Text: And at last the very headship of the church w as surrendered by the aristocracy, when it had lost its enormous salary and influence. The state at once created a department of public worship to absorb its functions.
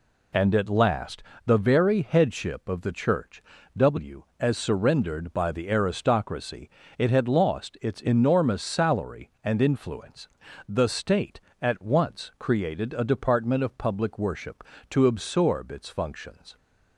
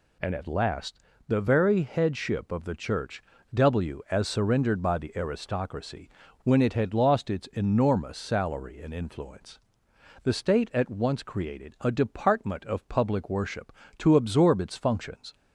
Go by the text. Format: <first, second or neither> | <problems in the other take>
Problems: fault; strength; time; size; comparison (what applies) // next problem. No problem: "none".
second | pauses between "last" and "the"; slight; at 1.2 s; 0.24 s long; slight in the second // pauses between "church" and "w"; slight; at 3.4 s; 0.36 s long; slight in the second // skips "when"; at 6.8 s